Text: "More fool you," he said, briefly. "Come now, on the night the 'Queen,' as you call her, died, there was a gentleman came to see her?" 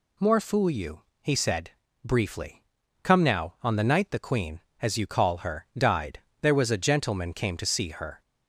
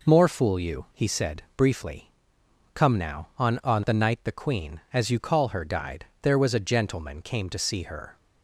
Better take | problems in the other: first | says "on" twice; at 3.6 s

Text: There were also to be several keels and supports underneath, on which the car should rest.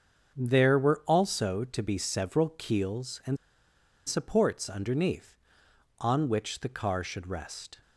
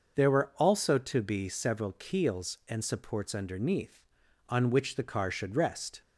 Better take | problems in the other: second | starts louder than the rest; until 1.3 s; 7 dB; noticeable in the second // pauses between "and" and "supports"; noticeable; at 3.3 s; 0.69 s long

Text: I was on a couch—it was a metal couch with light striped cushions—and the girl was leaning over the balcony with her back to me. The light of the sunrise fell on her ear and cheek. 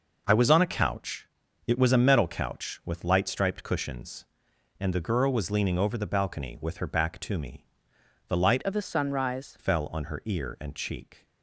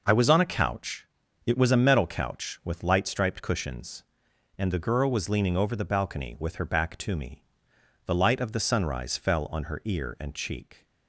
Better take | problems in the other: second | changes voice from "of" to "sunrise"; from 8.6 to 9.5 s; 0.9 s long

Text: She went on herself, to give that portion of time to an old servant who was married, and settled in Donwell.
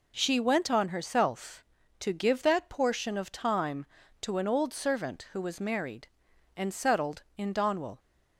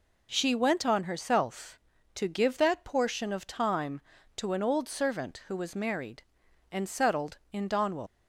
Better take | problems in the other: first | leaves "Donwell" unfinished; at 8.0 s; 75 ms

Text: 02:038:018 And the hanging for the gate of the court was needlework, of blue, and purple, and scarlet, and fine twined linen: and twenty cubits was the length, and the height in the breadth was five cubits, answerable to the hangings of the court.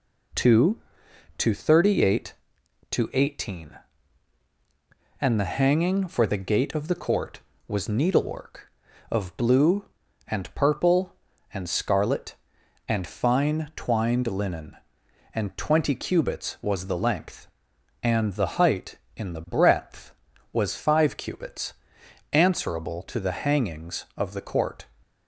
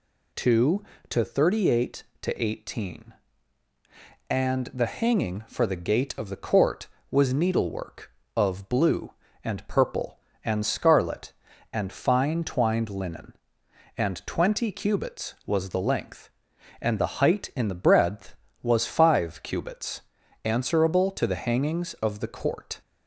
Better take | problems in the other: neither | none

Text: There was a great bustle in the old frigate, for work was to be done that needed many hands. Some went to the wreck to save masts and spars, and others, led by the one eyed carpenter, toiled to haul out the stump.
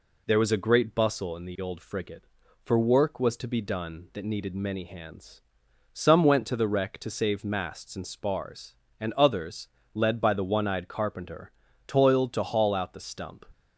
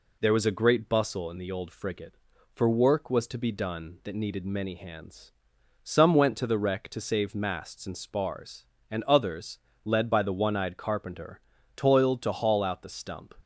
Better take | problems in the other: neither | none

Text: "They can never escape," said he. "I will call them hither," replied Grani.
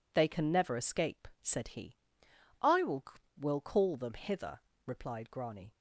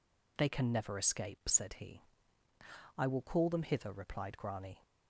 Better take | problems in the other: second | says "will" twice; at 3.3 s

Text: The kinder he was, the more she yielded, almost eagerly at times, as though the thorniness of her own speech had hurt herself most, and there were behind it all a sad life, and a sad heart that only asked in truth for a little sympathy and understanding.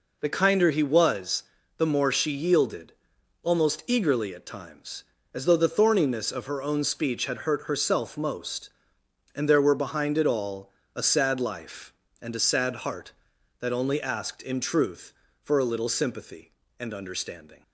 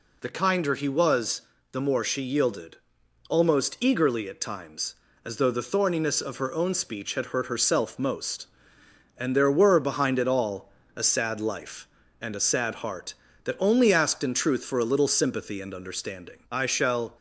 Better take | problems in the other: first | pauses between "all" and "a"; slight; at 10.7 s; 0.24 s long; slight in the first // goes on to say "I shall"; noticeable; from 16.5 s on; 0.66 s long

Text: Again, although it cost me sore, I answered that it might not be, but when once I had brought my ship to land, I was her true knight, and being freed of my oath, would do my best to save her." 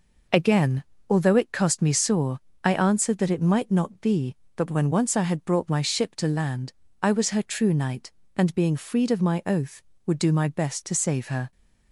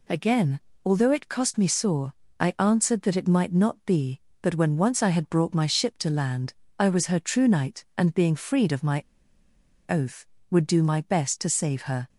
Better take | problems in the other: first | pauses between "my" and "oath"; noticeable; at 9.0 s; 0.85 s long

